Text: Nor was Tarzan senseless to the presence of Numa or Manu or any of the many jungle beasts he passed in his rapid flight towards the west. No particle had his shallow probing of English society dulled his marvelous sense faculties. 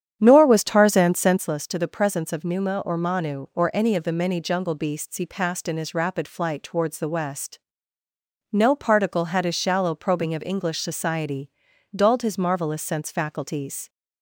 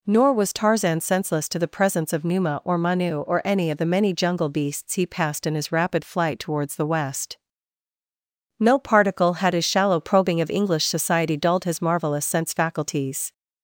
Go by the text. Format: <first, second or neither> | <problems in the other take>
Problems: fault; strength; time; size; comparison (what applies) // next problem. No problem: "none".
second | starts louder than the rest; strong; until 1.5 s; 9 dB // pauses between "society" and "dulled"; at 11.5 s; 0.42 s long